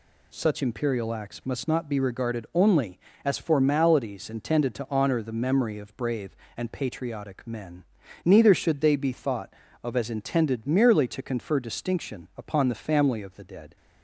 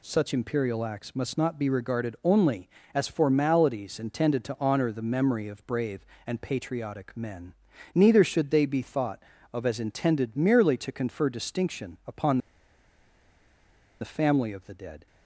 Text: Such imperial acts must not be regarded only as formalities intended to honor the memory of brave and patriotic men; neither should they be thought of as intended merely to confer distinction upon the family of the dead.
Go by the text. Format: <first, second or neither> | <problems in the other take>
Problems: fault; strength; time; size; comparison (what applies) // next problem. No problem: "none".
first | pauses between "upon" and "the"; strong; at 12.3 s; 1.6 s long